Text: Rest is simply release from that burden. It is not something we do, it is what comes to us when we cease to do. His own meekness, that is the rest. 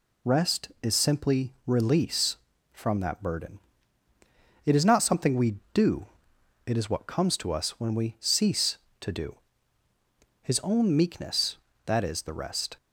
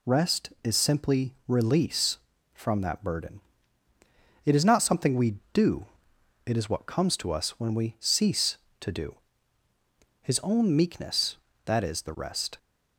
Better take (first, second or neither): neither